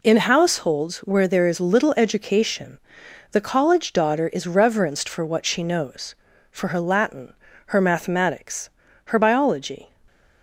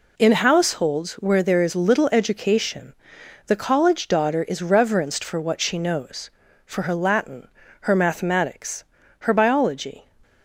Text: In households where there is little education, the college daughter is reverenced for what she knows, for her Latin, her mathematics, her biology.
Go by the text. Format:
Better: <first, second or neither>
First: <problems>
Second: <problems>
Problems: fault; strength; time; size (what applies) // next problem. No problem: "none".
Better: neither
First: none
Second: none